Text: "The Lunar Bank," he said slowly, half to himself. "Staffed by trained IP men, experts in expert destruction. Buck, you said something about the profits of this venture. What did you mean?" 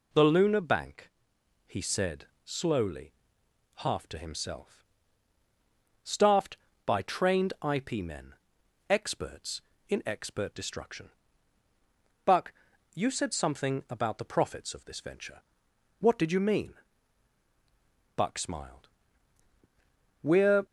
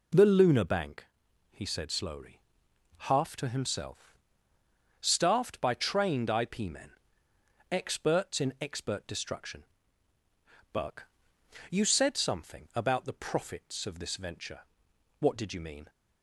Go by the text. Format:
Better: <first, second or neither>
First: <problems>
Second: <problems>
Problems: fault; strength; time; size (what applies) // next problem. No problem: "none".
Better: second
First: pauses between "said" and "slowly"; slight; at 2.2 s; 0.18 s long // goes on to say "Buck smiled We're"; strong; from 18.1 s on; 2.4 s long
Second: none